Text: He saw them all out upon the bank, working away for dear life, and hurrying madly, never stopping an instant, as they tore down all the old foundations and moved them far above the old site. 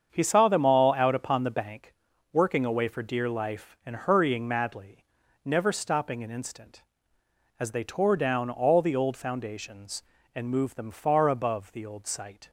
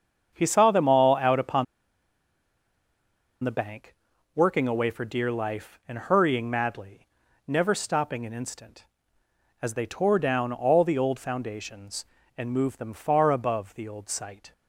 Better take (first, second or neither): first